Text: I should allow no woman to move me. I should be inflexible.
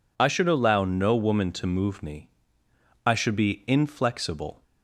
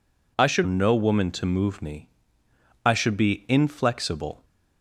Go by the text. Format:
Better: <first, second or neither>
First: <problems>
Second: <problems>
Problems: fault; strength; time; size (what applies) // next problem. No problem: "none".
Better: first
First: none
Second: skips "allow"; at 0.6 s